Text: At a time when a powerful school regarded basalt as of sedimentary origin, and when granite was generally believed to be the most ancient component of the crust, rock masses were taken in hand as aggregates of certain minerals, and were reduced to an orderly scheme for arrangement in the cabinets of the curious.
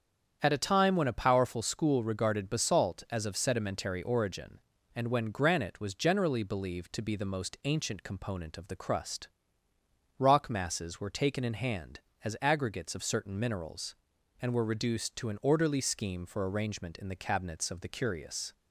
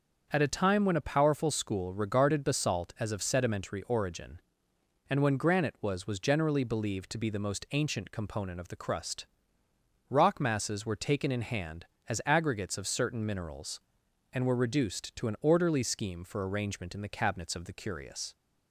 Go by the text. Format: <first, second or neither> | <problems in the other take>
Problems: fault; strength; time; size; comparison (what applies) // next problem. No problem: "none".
first | starts louder than the rest; until 1.3 s; 7 dB; strong in the first // says "was" twice; at 6.0 s